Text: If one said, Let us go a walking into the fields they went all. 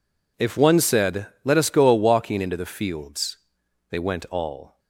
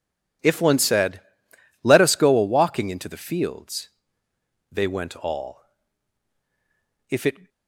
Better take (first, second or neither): first